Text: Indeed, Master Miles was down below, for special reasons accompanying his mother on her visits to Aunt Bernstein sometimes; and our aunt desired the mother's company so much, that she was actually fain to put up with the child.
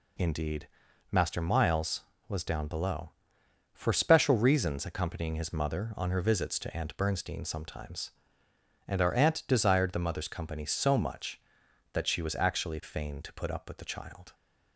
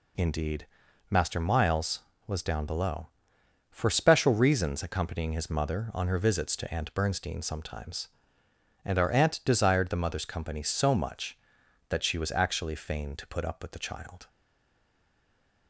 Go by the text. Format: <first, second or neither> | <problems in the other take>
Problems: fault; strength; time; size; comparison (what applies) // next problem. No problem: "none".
first | stays silent after the last word; noticeable; from 14.2 s on; 1.4 s long